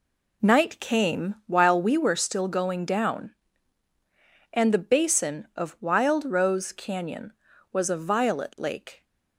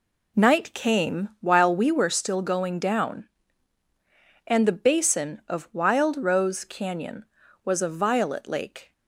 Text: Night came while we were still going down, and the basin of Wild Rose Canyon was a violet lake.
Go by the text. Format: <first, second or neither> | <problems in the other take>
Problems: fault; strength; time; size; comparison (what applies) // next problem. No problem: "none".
neither | none